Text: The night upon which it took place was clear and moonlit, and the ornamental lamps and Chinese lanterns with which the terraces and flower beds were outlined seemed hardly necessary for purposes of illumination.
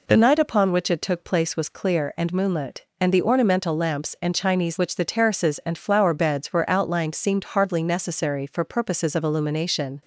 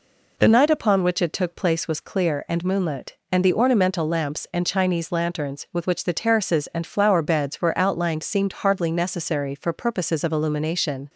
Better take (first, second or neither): second